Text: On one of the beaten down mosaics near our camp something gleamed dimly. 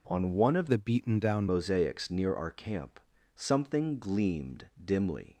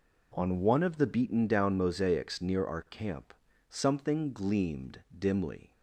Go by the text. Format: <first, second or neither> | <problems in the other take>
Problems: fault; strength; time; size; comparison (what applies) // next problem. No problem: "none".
second | changes voice from "the" to "down"; from 0.7 to 1.4 s; 0.7 s long // pauses between "camp" and "something"; at 2.9 s; 0.38 s long; also in the second // pauses between "gleamed" and "dimly"; slight; at 4.6 s; 0.18 s long; slight in the second